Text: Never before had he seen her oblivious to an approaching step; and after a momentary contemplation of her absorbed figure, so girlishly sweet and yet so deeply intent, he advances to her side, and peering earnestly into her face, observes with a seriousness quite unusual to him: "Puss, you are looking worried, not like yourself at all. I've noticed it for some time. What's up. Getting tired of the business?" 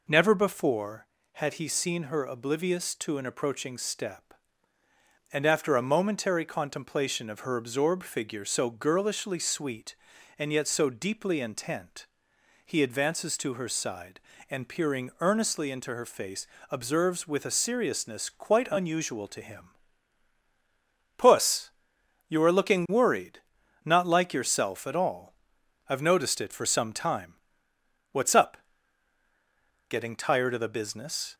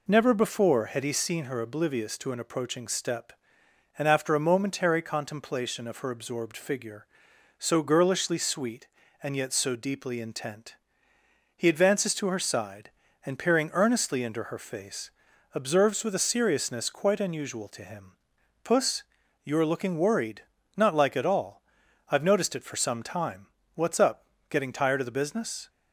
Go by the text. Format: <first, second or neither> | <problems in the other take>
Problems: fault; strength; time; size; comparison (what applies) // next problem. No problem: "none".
first | skips "yourself"; at 21.1 s